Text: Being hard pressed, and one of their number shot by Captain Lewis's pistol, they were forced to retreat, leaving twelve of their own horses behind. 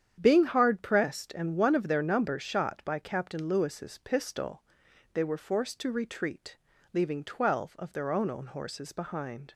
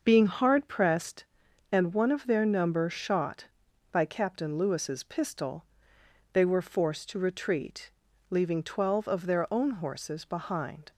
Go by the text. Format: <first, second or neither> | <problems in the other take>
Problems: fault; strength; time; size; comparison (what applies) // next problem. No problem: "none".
second | starts louder than the rest; strong; until 1.2 s; 9 dB; also in the second // says "own" twice; at 8.2 s